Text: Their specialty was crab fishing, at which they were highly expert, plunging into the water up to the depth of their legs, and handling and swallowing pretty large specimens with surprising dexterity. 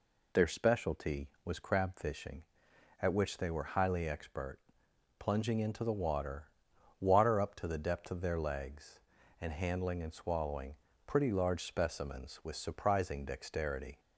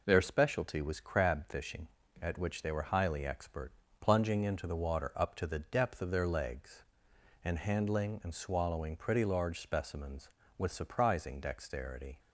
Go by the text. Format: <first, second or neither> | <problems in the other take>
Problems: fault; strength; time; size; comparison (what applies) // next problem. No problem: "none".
second | says "water" twice; at 7.0 s // pauses between "swallowing" and "pretty"; slight; at 10.7 s; 0.30 s long